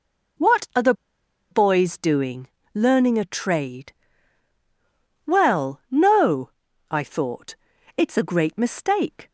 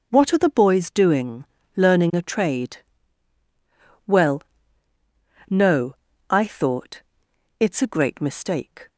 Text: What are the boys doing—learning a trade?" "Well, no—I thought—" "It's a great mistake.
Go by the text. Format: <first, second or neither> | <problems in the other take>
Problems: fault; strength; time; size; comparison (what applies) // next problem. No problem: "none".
second | pauses between "the" and "boys"; noticeable; at 0.9 s; 0.58 s long